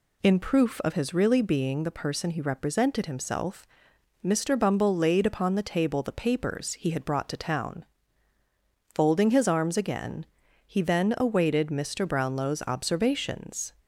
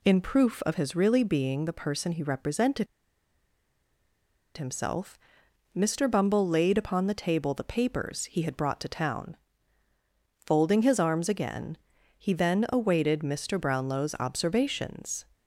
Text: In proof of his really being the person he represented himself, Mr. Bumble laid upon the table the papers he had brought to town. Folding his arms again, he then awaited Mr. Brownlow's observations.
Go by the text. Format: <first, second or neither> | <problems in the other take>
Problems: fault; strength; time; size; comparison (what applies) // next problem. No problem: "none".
first | pauses between "represented" and "himself"; strong; at 2.8 s; 1.7 s long